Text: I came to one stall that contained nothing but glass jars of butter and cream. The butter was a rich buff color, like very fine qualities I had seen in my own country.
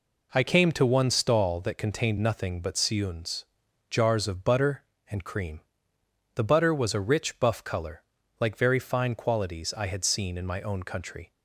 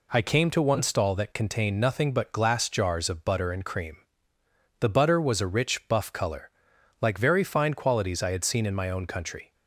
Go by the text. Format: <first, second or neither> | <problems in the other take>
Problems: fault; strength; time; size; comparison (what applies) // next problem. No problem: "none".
second | says "siuns" for "glass"; at 2.7 s